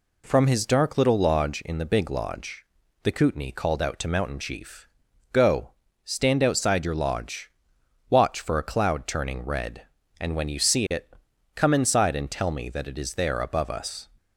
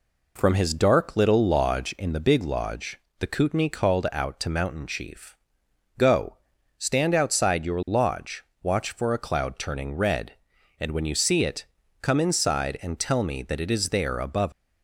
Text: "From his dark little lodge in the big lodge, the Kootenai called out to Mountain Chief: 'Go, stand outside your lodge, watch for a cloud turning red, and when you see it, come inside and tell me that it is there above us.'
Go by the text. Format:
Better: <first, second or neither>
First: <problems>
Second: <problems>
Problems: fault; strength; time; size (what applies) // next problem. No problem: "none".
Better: first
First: none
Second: stops before "us"; at 14.5 s